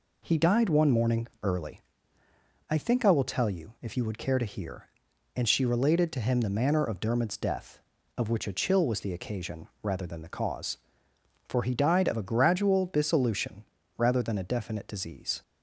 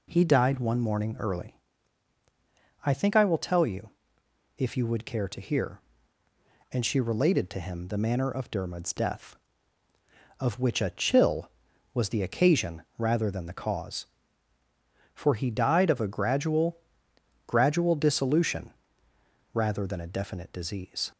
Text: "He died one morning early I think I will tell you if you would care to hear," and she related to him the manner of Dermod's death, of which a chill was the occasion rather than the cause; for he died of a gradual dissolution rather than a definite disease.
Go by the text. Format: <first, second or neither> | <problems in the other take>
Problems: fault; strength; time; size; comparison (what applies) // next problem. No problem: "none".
first | pauses between "early" and "I"; strong; at 1.5 s; 1.3 s long; noticeable in the first // pauses between "you" and "if"; noticeable; at 3.9 s; 0.66 s long // pauses between "occasion" and "rather"; slight; at 12.8 s; 0.16 s long // says "gradual" twice; at 17.4 s // pauses between "dissolution" and "rather"; noticeable; at 18.7 s; 0.80 s long; slight in the first